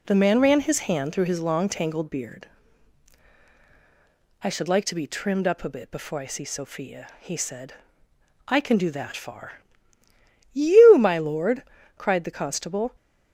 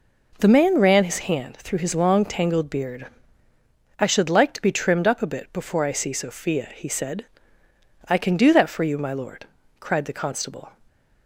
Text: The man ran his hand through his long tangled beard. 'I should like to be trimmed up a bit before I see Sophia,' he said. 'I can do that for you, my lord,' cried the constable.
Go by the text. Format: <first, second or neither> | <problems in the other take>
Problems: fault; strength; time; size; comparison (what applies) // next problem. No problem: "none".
second | says "far" for "for"; at 9.1 s